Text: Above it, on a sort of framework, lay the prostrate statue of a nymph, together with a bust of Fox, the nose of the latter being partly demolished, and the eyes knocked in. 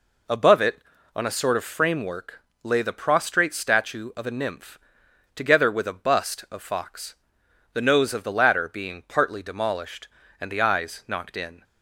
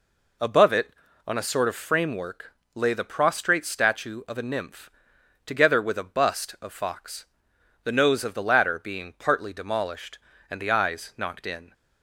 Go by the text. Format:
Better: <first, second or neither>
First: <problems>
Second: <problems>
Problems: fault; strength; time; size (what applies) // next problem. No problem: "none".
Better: neither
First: none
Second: none